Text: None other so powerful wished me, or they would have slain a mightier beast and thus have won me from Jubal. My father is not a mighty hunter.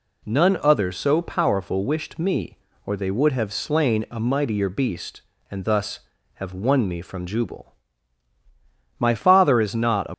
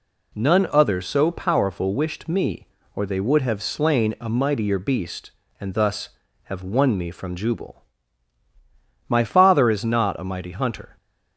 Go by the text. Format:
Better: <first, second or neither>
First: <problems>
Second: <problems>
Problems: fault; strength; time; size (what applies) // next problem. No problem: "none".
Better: second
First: stops before "mighty hunter"; at 10.1 s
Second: none